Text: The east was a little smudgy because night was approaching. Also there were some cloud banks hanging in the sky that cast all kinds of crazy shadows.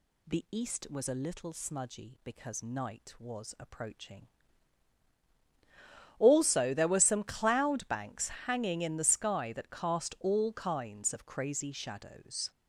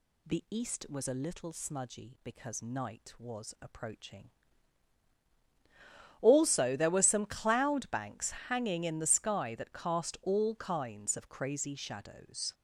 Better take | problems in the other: neither | pauses between "banks" and "hanging"; slight; the same in both

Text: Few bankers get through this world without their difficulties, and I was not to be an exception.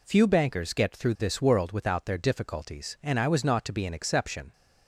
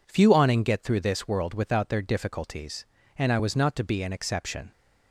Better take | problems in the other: first | says "awning" for "bankers"; at 0.3 s

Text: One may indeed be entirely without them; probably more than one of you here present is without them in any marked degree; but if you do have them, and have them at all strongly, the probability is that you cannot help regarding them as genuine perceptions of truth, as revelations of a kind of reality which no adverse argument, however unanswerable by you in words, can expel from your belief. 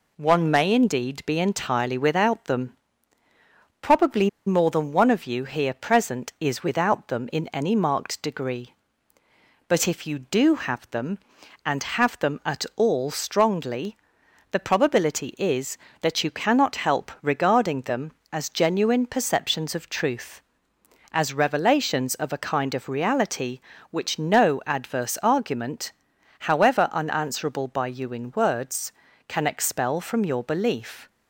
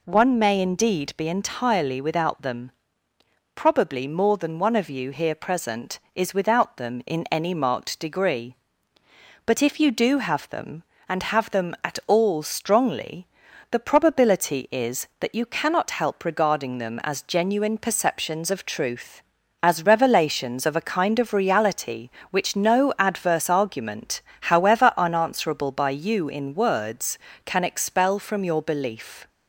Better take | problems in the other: second | pauses between "probably" and "more"; slight; at 4.2 s; 0.17 s long

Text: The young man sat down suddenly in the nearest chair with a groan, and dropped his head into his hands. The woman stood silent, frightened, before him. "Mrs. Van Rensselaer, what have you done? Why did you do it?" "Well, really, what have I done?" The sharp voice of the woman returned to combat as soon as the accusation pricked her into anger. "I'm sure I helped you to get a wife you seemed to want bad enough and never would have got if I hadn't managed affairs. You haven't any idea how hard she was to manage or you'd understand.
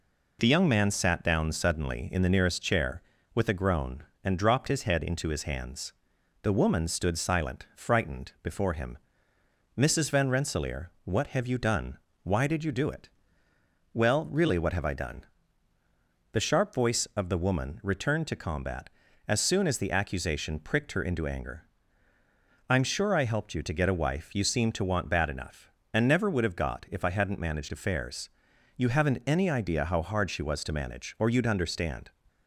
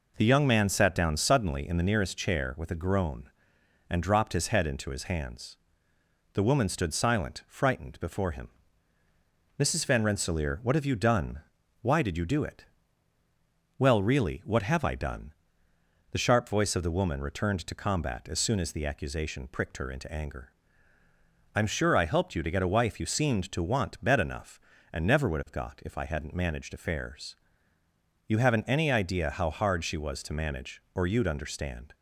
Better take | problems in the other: first | says "bed" for "bad"; at 24.0 s

